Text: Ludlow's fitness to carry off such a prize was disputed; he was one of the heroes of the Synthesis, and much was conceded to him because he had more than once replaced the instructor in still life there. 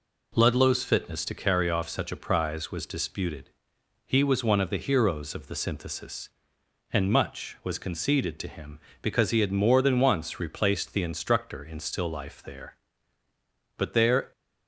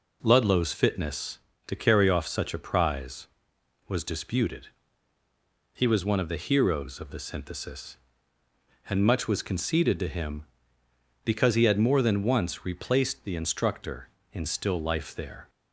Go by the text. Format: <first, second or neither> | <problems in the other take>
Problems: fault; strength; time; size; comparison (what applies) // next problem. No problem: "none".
second | goes on to say "But there"; from 13.7 s on; 0.54 s long